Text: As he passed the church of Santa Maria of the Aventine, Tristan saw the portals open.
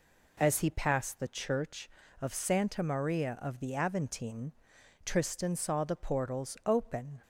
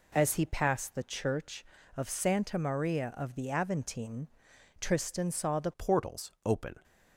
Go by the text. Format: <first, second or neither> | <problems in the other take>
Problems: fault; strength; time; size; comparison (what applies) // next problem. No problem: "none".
first | changes voice at "portals"; from 5.7 s on; 1.1 s long